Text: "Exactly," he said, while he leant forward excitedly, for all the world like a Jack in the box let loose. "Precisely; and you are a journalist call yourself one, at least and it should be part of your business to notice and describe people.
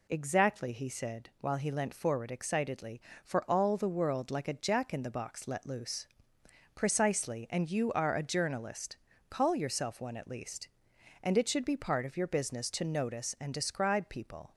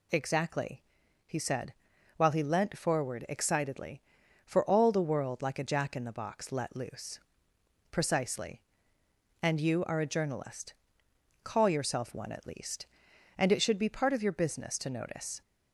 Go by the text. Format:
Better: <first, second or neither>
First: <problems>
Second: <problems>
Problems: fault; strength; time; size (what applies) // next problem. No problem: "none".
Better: first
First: pauses between "journalist" and "call"; slight; at 8.9 s; 0.32 s long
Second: pauses between "journalist" and "call"; noticeable; at 10.7 s; 0.68 s long // stops before "and describe people"; at 15.4 s